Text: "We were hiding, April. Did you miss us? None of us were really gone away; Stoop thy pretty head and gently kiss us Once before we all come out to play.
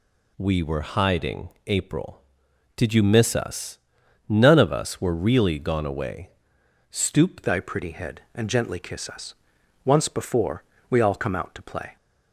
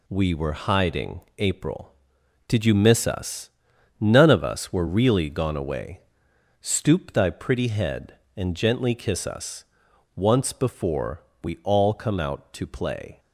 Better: second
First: changes voice at "thy"; from 7.4 s on; 4.5 s long // pauses between "us" and "Once"; noticeable; at 9.3 s; 0.50 s long // pauses between "before" and "we"; slight; at 10.6 s; 0.28 s long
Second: pauses between "us" and "Once"; noticeable; at 9.6 s; 0.50 s long // pauses between "before" and "we"; slight; at 11.2 s; 0.22 s long

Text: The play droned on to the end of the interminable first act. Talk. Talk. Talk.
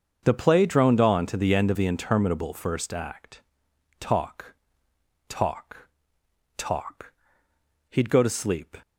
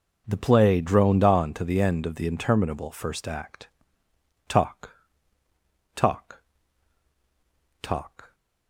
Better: second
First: starts louder than the rest; until 1.2 s; 6.5 dB // goes on to say "He'd go to sleep"; noticeable; from 7.8 s on; 0.88 s long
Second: none

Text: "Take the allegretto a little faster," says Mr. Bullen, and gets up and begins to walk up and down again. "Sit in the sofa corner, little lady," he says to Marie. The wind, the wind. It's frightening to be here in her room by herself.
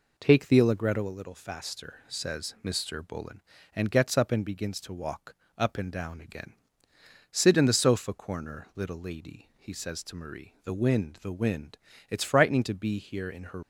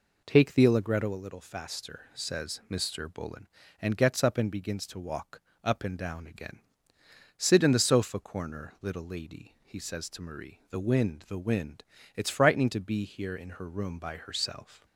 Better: second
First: pauses between "walk" and "up"; slight; at 5.3 s; 0.22 s long // stops before "room by herself"; at 13.6 s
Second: pauses between "walk" and "up"; slight; at 5.4 s; 0.22 s long

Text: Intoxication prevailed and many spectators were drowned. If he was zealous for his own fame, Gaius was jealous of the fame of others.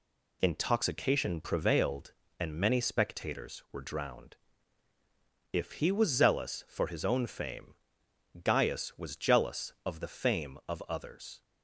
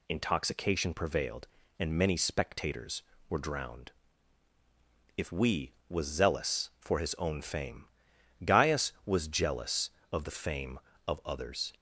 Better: first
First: none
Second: says "we" for "he"; at 5.3 s

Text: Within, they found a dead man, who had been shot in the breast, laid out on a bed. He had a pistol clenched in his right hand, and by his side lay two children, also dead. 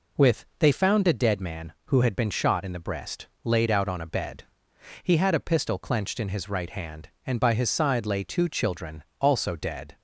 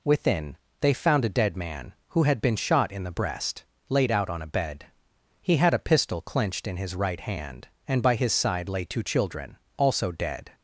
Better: second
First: says "With" for "Within"; at 0.1 s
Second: none

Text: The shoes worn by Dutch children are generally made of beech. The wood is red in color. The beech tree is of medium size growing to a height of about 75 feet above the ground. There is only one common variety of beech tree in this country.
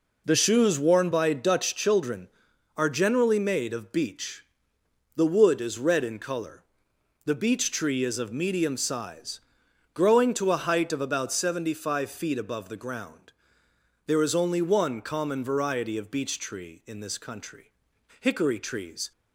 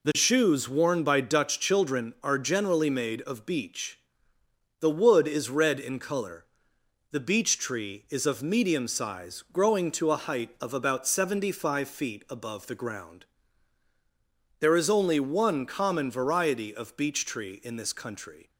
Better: second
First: pauses between "size" and "growing"; noticeable; at 9.4 s; 0.52 s long // goes on to say "Hickory trees"; noticeable; from 18.1 s on; 0.92 s long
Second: none

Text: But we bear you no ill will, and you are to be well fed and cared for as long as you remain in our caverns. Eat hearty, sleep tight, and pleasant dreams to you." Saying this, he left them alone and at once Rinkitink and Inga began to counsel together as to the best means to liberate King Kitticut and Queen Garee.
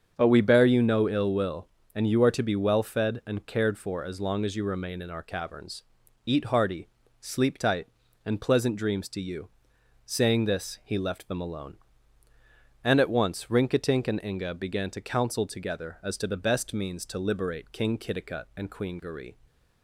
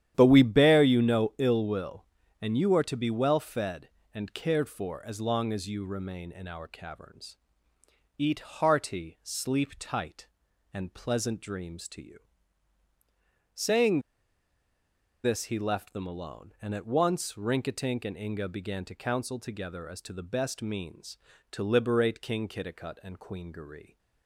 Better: first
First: starts louder than the rest; strong; until 1.1 s; 7.5 dB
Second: starts louder than the rest; strong; until 1.1 s; 10.5 dB // pauses between "Saying" and "this"; at 13.9 s; 1.2 s long

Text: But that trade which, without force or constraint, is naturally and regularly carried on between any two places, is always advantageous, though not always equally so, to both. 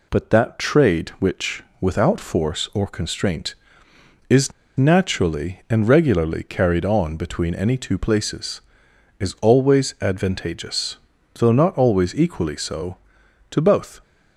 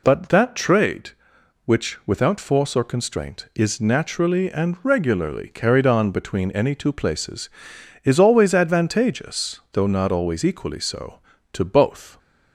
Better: second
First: pauses between "is" and "naturally"; slight; at 4.5 s; 0.26 s long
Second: none

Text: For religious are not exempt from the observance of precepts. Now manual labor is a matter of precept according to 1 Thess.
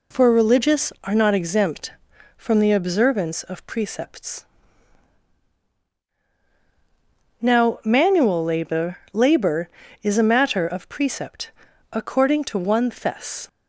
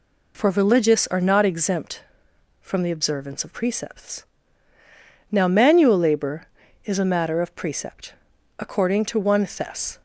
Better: second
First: says "labor" twice; at 9.1 s // pauses between "precept" and "according"; at 11.5 s; 0.42 s long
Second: pauses between "precept" and "according"; noticeable; at 8.1 s; 0.46 s long

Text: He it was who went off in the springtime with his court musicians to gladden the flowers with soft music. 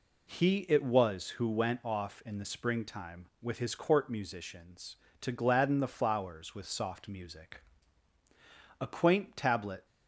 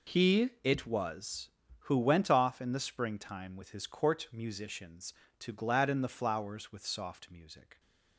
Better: second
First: goes on to say "A quaint tablet"; noticeable; from 8.8 s on; 1.0 s long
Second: none

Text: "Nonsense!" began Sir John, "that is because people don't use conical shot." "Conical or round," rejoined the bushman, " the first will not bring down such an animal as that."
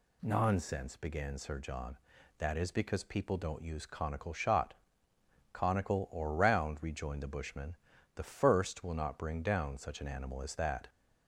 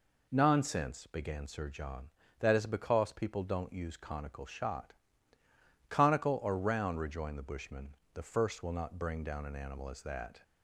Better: first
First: none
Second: skips "such"; at 9.4 s

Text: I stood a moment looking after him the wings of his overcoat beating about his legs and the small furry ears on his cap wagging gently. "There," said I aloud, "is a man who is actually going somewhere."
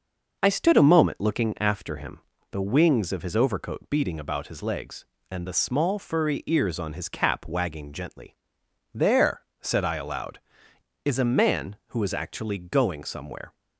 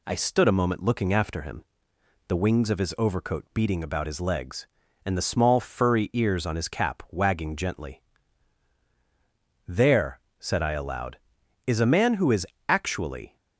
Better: first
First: pauses between "him" and "the"; slight; at 2.1 s; 0.32 s long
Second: pauses between "him" and "the"; noticeable; at 1.6 s; 0.64 s long // pauses between "is" and "actually"; slight; at 12.4 s; 0.20 s long // stops before "going somewhere"; at 13.3 s

